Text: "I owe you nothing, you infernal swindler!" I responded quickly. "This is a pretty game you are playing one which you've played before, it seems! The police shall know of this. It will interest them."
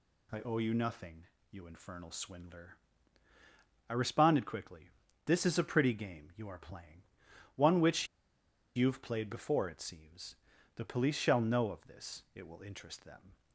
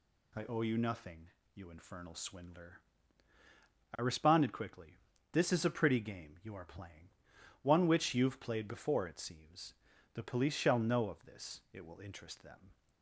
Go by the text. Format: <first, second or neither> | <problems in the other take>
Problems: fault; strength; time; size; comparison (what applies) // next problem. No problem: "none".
second | pauses between "playing" and "one"; noticeable; at 7.0 s; 0.54 s long; noticeable in the second // pauses between "which" and "you've"; noticeable; at 8.0 s; 0.69 s long